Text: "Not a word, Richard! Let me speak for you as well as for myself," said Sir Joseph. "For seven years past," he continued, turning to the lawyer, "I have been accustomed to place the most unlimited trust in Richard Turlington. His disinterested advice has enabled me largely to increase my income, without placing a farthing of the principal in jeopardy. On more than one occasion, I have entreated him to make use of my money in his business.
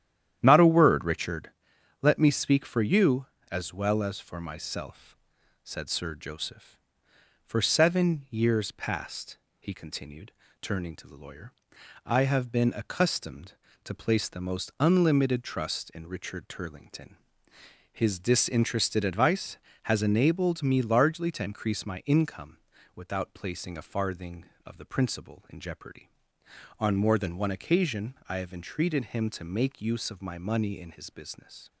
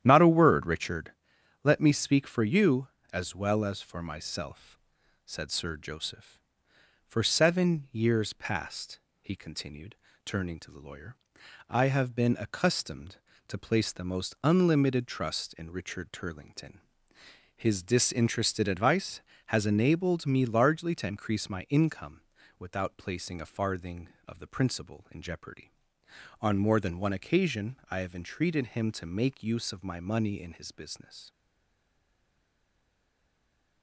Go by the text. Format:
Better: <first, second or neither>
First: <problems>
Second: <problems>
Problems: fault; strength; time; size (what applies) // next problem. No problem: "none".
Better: first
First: starts louder than the rest; strong; until 1.4 s; 10.5 dB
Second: starts louder than the rest; strong; until 1.0 s; 10.5 dB // stays silent after the last word; from 31.3 s on; 2.5 s long